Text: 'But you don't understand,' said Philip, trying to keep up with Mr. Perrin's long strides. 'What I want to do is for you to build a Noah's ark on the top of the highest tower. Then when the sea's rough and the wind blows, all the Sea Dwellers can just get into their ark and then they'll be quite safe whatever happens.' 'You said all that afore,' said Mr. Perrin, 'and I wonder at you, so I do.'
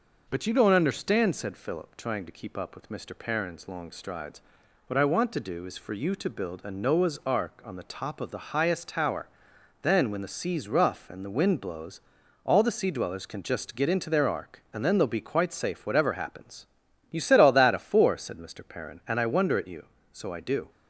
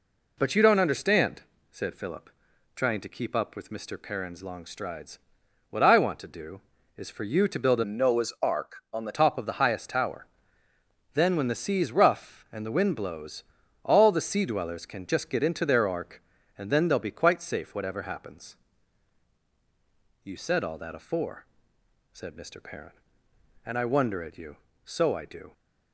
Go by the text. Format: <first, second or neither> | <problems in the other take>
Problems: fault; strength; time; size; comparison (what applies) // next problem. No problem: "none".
first | changes voice from "Noah's" to "the"; from 7.8 to 9.1 s; 1.3 s long